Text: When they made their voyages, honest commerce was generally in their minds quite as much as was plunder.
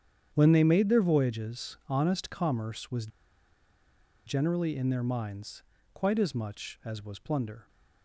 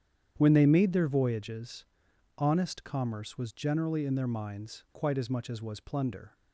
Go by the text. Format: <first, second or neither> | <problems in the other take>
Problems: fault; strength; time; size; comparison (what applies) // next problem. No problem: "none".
second | starts louder than the rest; strong; until 1.3 s; 8.5 dB; strong in the second // pauses between "was" and "generally"; at 3.0 s; 1.1 s long // pauses between "minds" and "quite"; slight; at 5.6 s; 0.32 s long